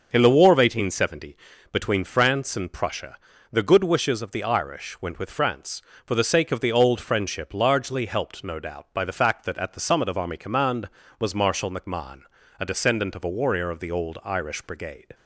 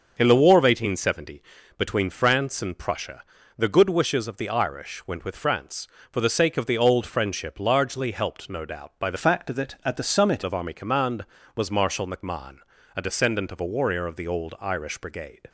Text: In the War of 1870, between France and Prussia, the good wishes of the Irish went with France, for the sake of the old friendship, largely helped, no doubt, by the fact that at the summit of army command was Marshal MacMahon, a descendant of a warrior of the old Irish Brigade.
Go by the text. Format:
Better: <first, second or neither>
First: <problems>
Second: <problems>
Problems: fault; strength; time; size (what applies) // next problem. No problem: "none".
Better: first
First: starts louder than the rest; until 1.1 s; 6.5 dB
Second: starts louder than the rest; until 1.1 s; 6.5 dB // changes voice from "fact" to "summit"; from 9.1 to 10.4 s; 1.3 s long